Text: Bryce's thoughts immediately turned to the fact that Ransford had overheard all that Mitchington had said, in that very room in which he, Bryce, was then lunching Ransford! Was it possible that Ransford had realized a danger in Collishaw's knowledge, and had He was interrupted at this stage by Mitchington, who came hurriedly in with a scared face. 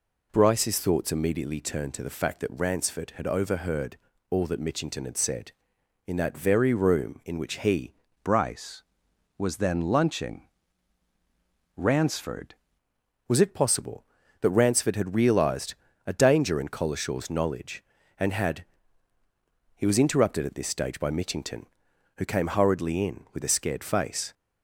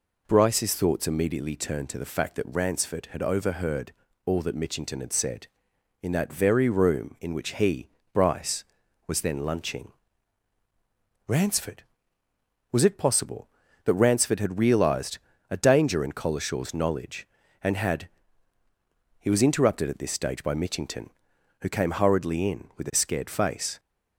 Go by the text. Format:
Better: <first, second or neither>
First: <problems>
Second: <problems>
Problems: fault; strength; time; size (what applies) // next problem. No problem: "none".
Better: second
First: pauses between "overheard" and "all"; slight; at 3.9 s; 0.34 s long // changes voice from "Bryce" to "Ransford"; from 8.2 to 12.5 s; 4.3 s long // pauses between "lunching" and "Ransford"; strong; at 10.4 s; 1.2 s long // pauses between "realized" and "a"; slight; at 15.7 s; 0.32 s long // pauses between "had" and "He"; at 18.6 s; 1.1 s long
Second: pauses between "overheard" and "all"; slight; at 3.9 s; 0.34 s long // pauses between "lunching" and "Ransford"; strong; at 9.9 s; 1.3 s long // pauses between "realized" and "a"; slight; at 15.1 s; 0.32 s long // pauses between "had" and "He"; at 18.0 s; 1.1 s long